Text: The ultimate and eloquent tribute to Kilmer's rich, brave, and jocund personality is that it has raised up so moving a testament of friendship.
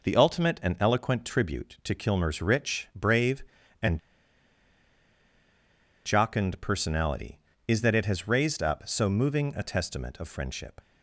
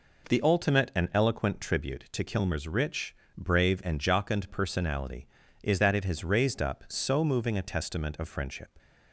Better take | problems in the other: second | pauses between "and" and "jocund"; strong; at 3.9 s; 2.0 s long

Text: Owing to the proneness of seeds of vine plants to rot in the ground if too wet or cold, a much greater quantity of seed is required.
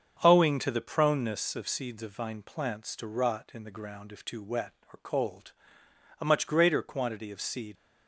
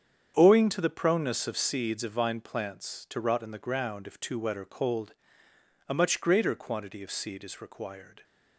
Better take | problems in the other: second | starts louder than the rest; until 1.2 s; 7 dB; strong in the second // stops before "is required"; at 7.7 s

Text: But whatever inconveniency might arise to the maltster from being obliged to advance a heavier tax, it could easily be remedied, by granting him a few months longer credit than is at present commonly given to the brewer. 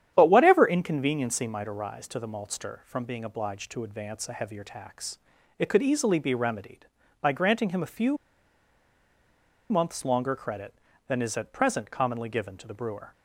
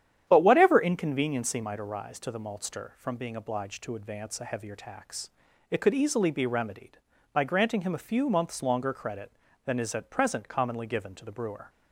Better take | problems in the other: second | starts louder than the rest; strong; until 1.1 s; 10 dB; strong in the second // pauses between "few" and "months"; strong; at 8.1 s; 1.5 s long

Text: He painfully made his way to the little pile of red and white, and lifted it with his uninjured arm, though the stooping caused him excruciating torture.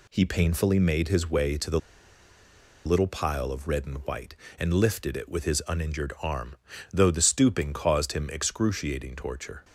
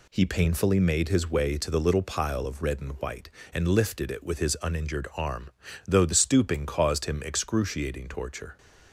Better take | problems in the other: second | pauses between "the" and "little"; at 1.7 s; 1.0 s long

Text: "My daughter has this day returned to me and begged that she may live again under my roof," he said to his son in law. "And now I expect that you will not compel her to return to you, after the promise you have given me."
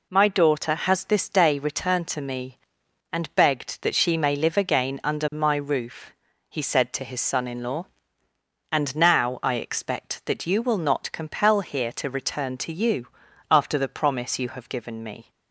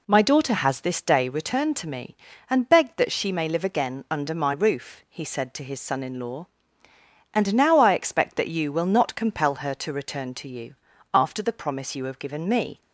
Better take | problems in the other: second | says "here" for "her"; at 11.5 s

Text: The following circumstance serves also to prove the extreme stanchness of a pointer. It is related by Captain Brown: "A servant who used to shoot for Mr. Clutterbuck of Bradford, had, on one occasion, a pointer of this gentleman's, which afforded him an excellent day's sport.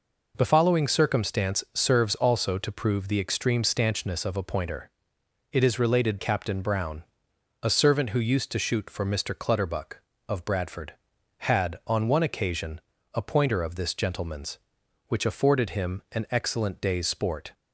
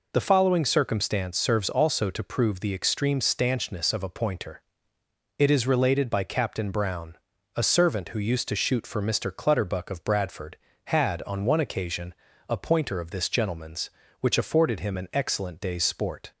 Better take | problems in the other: second | skips "by"; at 6.1 s

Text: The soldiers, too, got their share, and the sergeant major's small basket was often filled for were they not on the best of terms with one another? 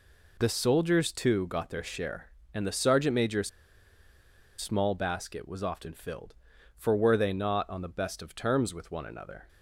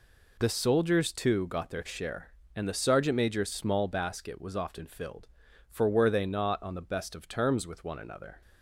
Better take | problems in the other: second | pauses between "major's" and "small"; at 3.4 s; 1.0 s long

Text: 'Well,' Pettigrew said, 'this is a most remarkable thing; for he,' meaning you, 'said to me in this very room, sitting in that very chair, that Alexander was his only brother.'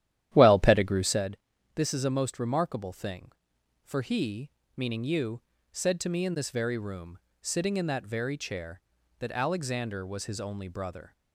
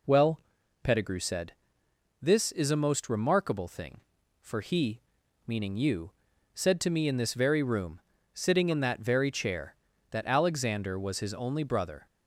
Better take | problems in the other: second | starts louder than the rest; strong; until 1.2 s; 12 dB

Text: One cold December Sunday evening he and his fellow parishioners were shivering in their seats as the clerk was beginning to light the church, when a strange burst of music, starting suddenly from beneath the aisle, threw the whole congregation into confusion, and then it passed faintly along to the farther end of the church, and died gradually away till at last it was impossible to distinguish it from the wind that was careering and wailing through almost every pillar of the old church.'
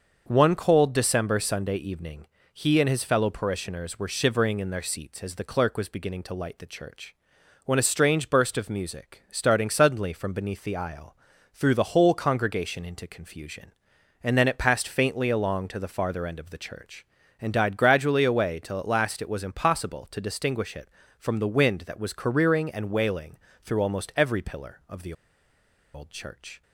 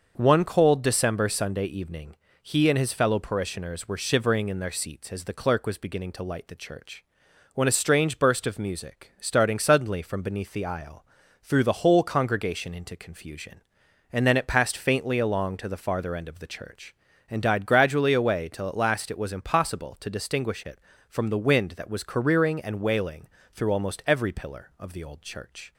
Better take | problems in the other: second | starts louder than the rest; until 1.2 s; 6 dB; also in the second // pauses between "evening" and "he"; slight; at 2.2 s; 0.26 s long; slight in the second // pauses between "wailing" and "through"; slight; at 23.3 s; 0.26 s long; slight in the second // pauses between "the" and "old"; noticeable; at 25.1 s; 0.81 s long

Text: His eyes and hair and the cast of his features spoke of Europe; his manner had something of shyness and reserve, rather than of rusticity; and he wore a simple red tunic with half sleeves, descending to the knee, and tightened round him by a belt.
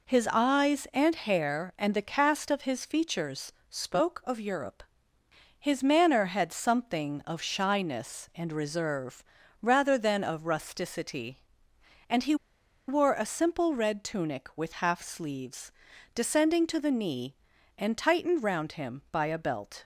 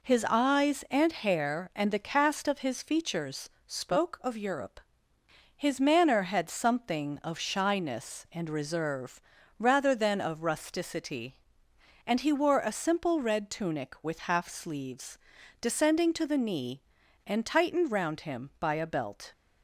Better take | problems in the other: second | pauses between "features" and "spoke"; slight; at 3.5 s; 0.18 s long; slight in the second // pauses between "he" and "wore"; noticeable; at 12.3 s; 0.53 s long

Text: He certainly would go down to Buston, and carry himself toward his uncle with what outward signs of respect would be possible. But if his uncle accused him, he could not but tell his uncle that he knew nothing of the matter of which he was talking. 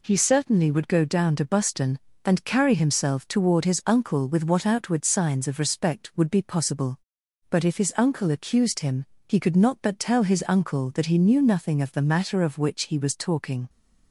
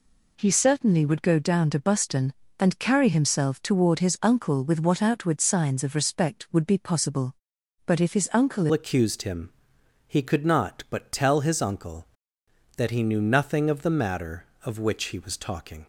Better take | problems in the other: first | changes voice at "accused"; from 8.7 s on; 7.1 s long

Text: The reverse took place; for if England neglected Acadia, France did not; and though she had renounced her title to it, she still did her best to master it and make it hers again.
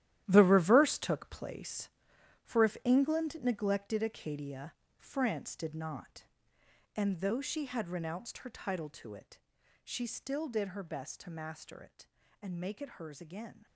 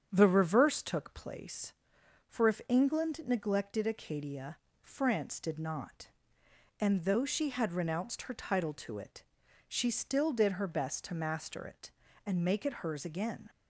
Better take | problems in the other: second | gets quieter; strong; throughout; 12 dB // starts louder than the rest; strong; until 1.2 s; 13 dB; strong in the second

